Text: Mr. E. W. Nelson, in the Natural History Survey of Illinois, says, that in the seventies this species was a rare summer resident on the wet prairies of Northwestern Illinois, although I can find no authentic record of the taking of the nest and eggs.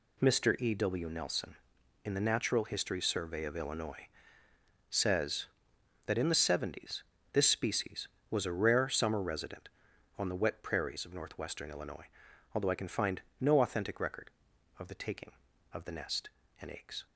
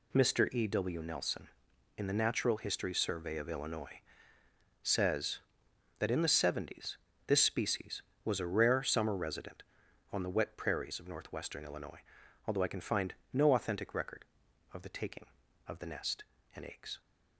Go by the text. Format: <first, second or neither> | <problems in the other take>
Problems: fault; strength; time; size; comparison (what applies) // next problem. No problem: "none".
neither | pauses between "seventies" and "this"; slight; the same in both // pauses between "find" and "no"; slight; the same in both